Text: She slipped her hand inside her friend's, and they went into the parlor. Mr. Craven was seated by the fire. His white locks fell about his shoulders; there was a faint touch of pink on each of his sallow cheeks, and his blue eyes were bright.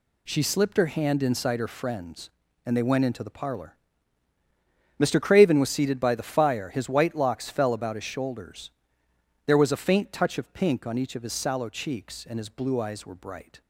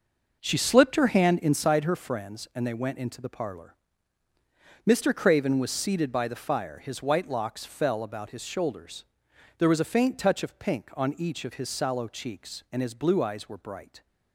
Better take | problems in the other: first | starts louder than the rest; noticeable; until 1.7 s; 6 dB

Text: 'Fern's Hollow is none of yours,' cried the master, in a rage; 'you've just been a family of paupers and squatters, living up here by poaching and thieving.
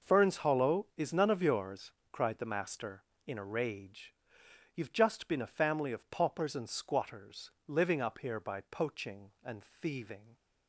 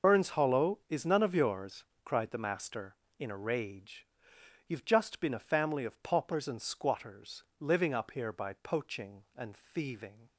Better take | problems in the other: first | loses the start of "Fern's"; at 0.0 s; 100 ms

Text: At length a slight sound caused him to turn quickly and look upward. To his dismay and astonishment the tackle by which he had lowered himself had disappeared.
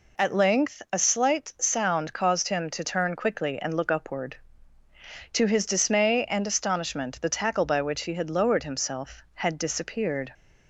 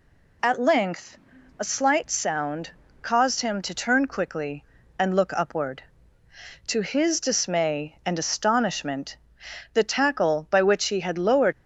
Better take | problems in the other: first | pauses between "length" and "a"; at 1.1 s; 0.40 s long // pauses between "sound" and "caused"; slight; at 2.6 s; 0.32 s long // pauses between "astonishment" and "the"; noticeable; at 9.1 s; 0.56 s long // stops before "himself had disappeared"; at 11.5 s

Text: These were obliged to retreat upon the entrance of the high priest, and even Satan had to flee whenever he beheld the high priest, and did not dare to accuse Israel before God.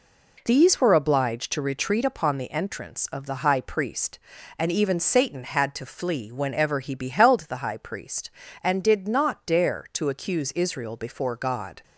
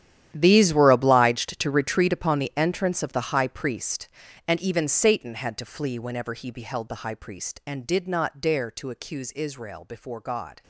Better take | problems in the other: first | gets quieter; strong; throughout; 16.5 dB

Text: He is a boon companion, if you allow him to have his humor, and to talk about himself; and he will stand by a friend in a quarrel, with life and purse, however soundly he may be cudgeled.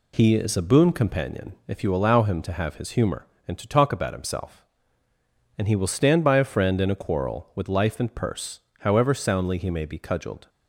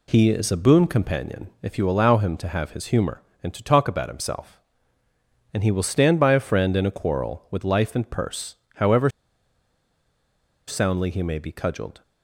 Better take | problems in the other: first | pauses between "however" and "soundly"; strong; at 9.1 s; 1.5 s long

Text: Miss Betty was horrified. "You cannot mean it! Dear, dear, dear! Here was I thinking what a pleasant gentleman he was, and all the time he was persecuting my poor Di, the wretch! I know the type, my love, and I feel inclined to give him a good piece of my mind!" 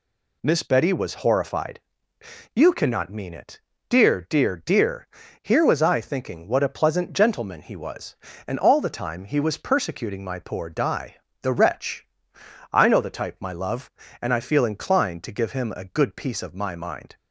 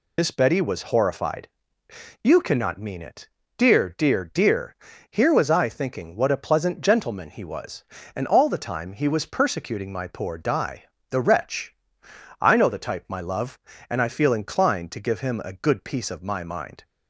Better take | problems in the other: first | loses the start of "Miss"; at 0.1 s; 85 ms

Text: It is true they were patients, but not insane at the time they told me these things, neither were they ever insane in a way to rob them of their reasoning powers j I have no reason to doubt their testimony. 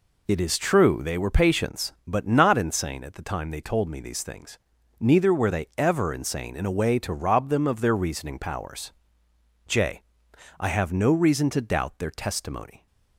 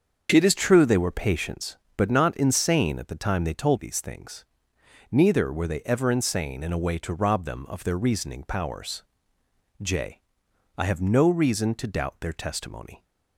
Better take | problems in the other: first | starts louder than the rest; until 1.3 s; 6.5 dB // skips "me"; at 3.7 s // pauses between "powers" and "j"; noticeable; at 9.0 s; 0.76 s long; noticeable in the first // pauses between "j" and "I"; noticeable; at 10.2 s; 0.54 s long; noticeable in the first

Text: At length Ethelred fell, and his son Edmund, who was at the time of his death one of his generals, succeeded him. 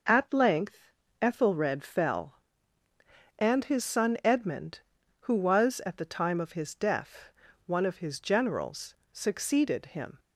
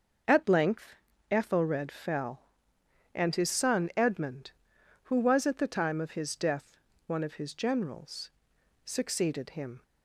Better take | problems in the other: neither | starts louder than the rest; the same in both // pauses between "length" and "Ethelred"; the same in both // pauses between "death" and "one"; slight; the same in both

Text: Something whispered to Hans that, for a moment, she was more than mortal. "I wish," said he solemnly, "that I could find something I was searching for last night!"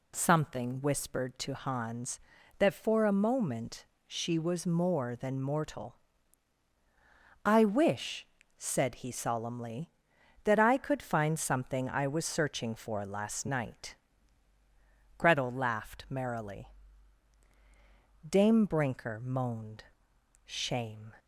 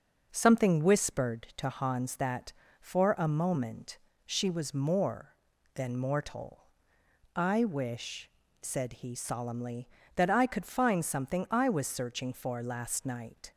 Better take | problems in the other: second | goes on to say "Gretel laughed merrily Dame Brinker moaned Shame"; strong; from 15.1 s on; 5.9 s long

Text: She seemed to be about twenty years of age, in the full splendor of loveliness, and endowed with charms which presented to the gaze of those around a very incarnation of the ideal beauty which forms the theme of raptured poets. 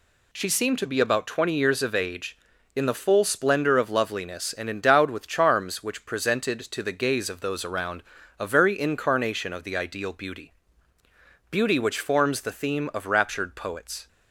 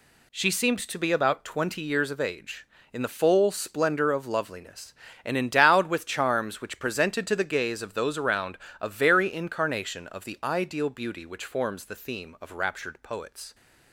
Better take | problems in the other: second | pauses between "around" and "a"; at 8.0 s; 0.38 s long; slight in the second // says "beauty" twice; at 11.5 s

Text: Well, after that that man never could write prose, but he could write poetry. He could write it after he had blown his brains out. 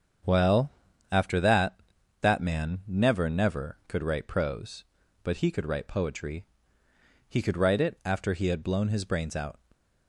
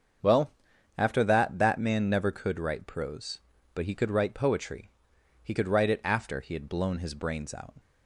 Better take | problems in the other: second | starts louder than the rest; strong; until 1.6 s; 7.5 dB; strong in the second // says "never" twice; at 3.2 s

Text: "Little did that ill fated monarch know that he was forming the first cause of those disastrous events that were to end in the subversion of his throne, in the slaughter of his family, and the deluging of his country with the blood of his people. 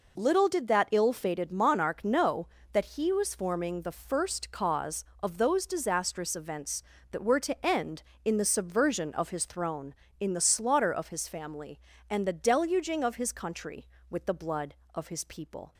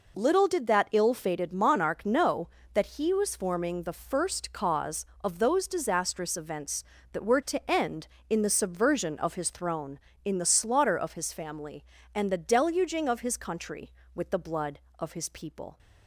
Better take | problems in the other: neither | none

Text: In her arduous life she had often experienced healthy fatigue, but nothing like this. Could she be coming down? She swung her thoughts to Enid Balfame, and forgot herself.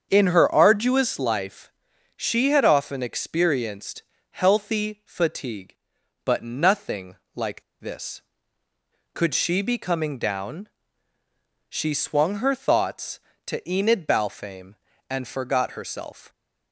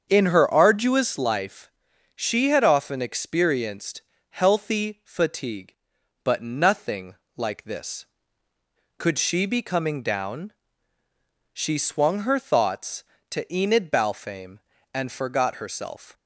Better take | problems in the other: second | starts louder than the rest; strong; until 1.1 s; 7.5 dB; strong in the second // pauses between "life" and "she"; noticeable; at 1.7 s; 0.46 s long; noticeable in the second // pauses between "experienced" and "healthy"; slight; at 4.0 s; 0.30 s long; slight in the second // pauses between "nothing" and "like"; slight; at 7.1 s; 0.20 s long; slight in the second // pauses between "like" and "this"; slight; at 7.6 s; 0.19 s long

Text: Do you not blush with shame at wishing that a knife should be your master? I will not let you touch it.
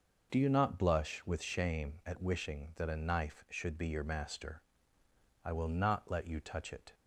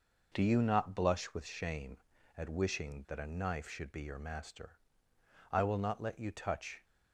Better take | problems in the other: first | stops before "it"; at 6.8 s

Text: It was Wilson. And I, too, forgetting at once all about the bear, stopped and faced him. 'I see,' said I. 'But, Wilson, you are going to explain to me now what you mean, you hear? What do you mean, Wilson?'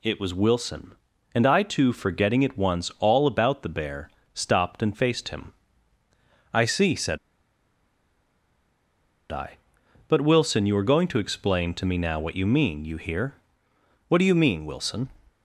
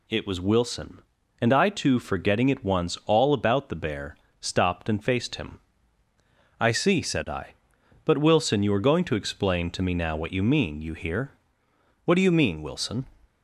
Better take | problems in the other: second | pauses between "said" and "I"; strong; at 7.1 s; 2.1 s long

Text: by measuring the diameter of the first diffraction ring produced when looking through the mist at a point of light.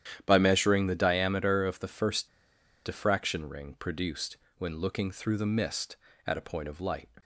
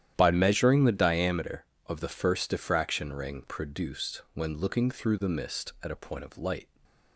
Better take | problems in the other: second | starts louder than the rest; strong; until 1.2 s; 10.5 dB; strong in the second // pauses between "first" and "diffraction"; noticeable; at 2.2 s; 0.56 s long // pauses between "produced" and "when"; slight; at 4.3 s; 0.22 s long

